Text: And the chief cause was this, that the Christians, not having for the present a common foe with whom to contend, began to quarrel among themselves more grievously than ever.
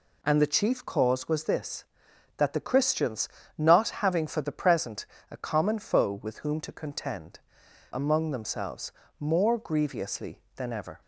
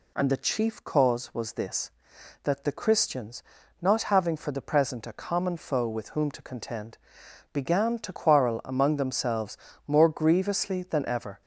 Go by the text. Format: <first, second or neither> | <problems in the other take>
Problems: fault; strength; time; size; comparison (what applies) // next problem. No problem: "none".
second | pauses between "present" and "a"; slight; at 5.0 s; 0.26 s long // skips "began to quarrel"; at 7.6 s // pauses between "themselves" and "more"; slight; at 8.9 s; 0.26 s long; slight in the second